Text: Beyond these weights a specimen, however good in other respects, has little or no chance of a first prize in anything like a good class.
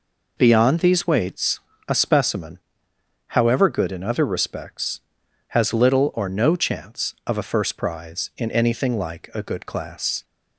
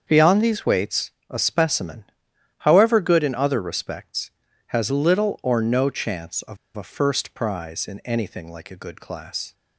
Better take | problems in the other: first | starts louder than the rest; until 1.0 s; 7 dB // pauses between "weights" and "a"; slight; at 1.0 s; 0.20 s long; slight in the first // pauses between "of" and "a"; slight; at 6.5 s; 0.18 s long

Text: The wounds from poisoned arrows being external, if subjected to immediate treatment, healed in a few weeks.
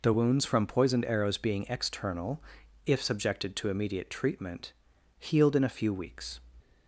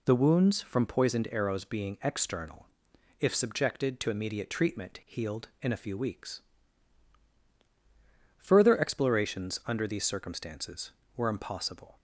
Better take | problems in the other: first | goes on to say "Further explorations under these circumstances were impossible"; strong; from 8.3 s on; 3.6 s long

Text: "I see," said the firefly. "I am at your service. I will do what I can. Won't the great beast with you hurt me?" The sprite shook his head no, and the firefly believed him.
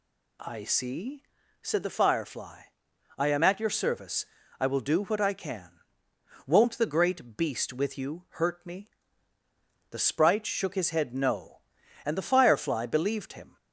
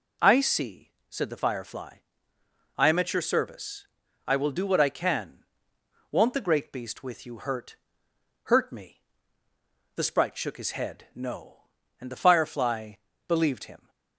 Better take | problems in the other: first | says "hurt" twice; at 8.4 s // pauses between "firefly" and "believed"; slight; at 12.9 s; 0.34 s long

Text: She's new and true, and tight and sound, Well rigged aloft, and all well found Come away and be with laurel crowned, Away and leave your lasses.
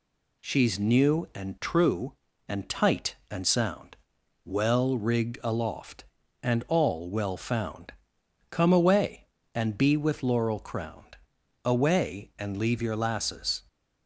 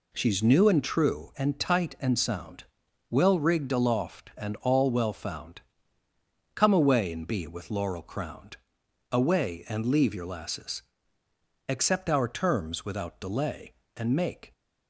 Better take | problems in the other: first | pauses between "found" and "Come"; noticeable; at 5.6 s; 0.92 s long; noticeable in the first // goes on to say "Accept our terms without delay And make"; strong; from 11.6 s on; 2.8 s long

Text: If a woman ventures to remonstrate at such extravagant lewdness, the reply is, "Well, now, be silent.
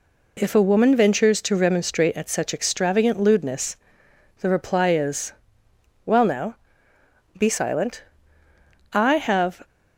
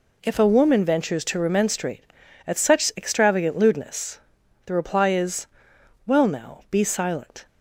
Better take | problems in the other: second | goes on to say "I have"; noticeable; from 8.9 s on; 0.74 s long

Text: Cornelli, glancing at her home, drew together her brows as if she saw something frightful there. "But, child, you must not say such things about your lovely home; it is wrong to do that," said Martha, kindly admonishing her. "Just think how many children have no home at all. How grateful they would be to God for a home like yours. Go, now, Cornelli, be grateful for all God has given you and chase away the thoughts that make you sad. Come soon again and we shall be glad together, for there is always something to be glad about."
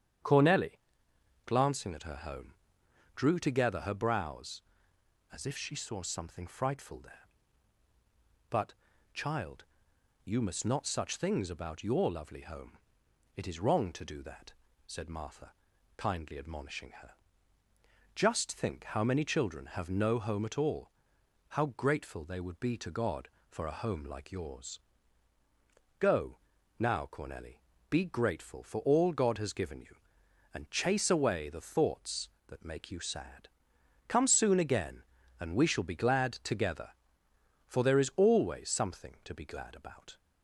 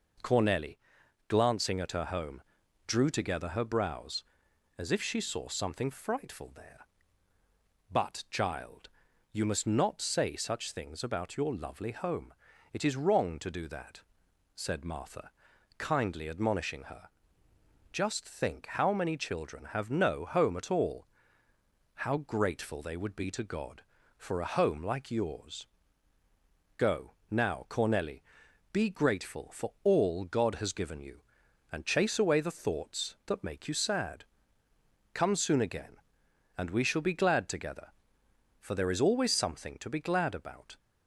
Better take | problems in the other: second | starts louder than the rest; strong; until 1.9 s; 9 dB // skips "say"; at 10.8 s

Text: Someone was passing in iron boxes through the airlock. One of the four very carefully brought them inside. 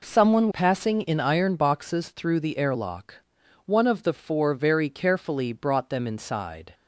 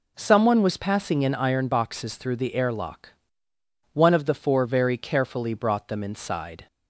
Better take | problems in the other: second | skips "was"; at 0.4 s

